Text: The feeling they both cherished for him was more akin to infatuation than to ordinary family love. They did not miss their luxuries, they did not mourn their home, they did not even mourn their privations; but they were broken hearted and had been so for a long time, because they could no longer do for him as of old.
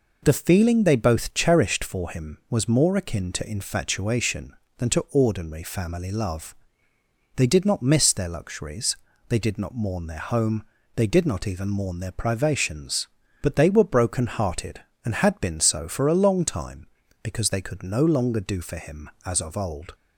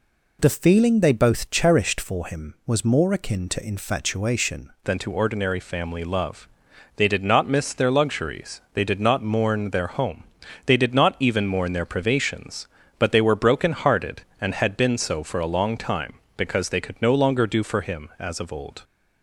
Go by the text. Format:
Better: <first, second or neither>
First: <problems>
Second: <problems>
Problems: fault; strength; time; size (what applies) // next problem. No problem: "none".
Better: first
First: none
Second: changes voice at "than"; from 4.8 s on; 14.0 s long